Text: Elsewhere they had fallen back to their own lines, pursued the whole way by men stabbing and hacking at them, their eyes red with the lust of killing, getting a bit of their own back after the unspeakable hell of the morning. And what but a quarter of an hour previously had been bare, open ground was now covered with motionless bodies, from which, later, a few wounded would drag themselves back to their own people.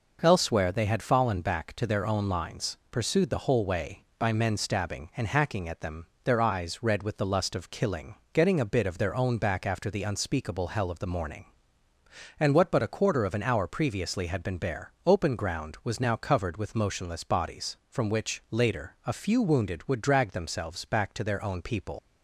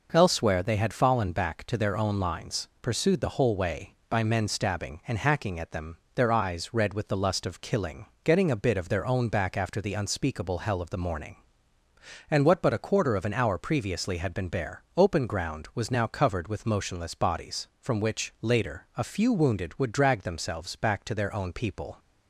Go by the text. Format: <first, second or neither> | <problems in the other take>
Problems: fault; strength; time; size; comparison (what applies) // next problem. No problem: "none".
second | leaves "people" unfinished; at 21.9 s; 90 ms